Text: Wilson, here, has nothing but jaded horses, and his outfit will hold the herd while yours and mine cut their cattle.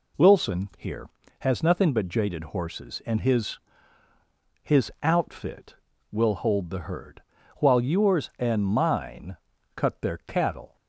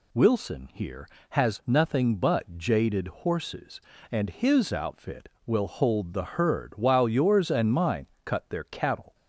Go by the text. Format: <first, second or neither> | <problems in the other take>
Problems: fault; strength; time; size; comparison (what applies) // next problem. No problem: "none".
second | says "his" twice; at 4.6 s // pauses between "herd" and "while"; slight; at 7.2 s; 0.36 s long // pauses between "mine" and "cut"; at 9.3 s; 0.40 s long; slight in the second